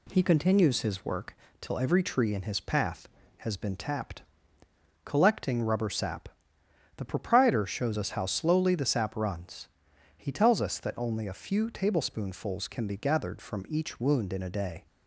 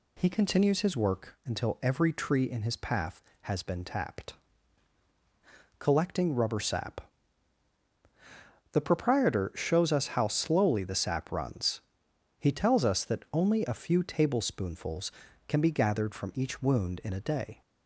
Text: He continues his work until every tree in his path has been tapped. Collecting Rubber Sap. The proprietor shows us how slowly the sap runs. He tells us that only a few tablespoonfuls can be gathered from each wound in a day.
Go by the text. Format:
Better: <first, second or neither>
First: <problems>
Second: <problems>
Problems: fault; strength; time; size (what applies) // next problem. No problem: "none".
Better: second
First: says "till" for "until"; at 1.5 s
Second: none